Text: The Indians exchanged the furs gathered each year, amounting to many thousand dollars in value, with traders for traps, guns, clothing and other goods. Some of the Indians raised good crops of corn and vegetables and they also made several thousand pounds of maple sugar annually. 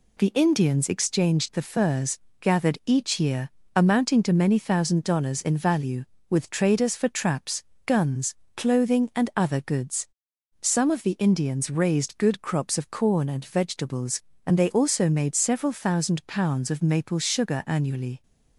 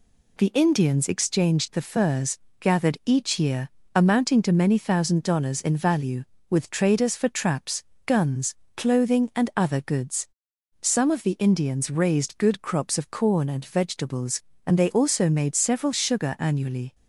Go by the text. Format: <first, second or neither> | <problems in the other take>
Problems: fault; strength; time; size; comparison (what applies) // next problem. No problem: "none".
first | pauses between "furs" and "gathered"; slight; at 2.3 s; 0.22 s long; slight in the first // skips "thousand pounds of maple"; at 15.9 s